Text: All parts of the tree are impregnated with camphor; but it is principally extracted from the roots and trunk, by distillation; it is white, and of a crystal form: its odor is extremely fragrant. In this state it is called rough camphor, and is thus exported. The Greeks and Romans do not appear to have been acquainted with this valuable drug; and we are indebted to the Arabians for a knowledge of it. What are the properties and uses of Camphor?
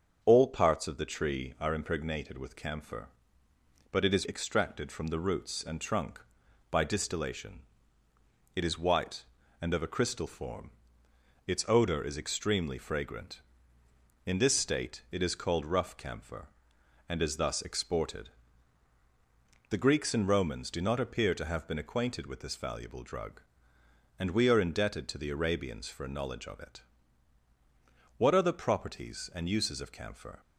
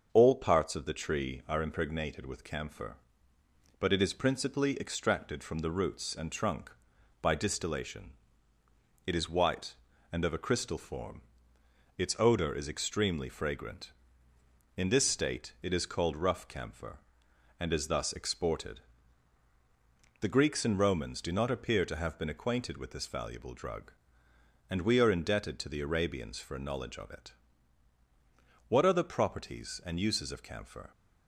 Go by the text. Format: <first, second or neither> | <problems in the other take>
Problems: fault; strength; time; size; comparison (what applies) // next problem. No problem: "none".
second | starts louder than the rest; until 1.2 s; 6.5 dB; also in the second // skips "principally"; at 4.2 s